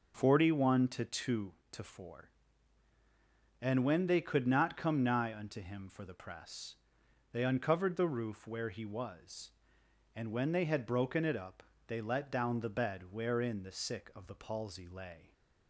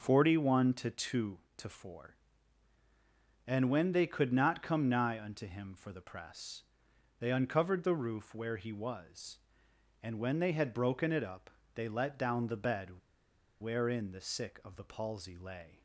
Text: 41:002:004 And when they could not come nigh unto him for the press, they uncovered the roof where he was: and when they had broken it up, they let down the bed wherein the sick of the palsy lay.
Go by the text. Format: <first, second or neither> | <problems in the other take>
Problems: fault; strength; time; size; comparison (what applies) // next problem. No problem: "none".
first | starts louder than the rest; noticeable; until 1.0 s; 6 dB; noticeable in the first // pauses between "bed" and "wherein"; noticeable; at 12.9 s; 0.61 s long